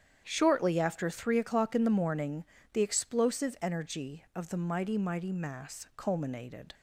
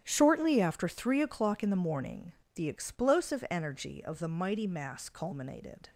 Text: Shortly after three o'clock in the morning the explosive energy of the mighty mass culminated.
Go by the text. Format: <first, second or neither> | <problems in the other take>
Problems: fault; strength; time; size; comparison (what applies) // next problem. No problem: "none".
second | starts louder than the rest; strong; until 1.2 s; 9 dB; strong in the second // pauses between "morning" and "the"; slight; at 2.4 s; 0.26 s long; slight in the second // says "mighty" twice; at 4.9 s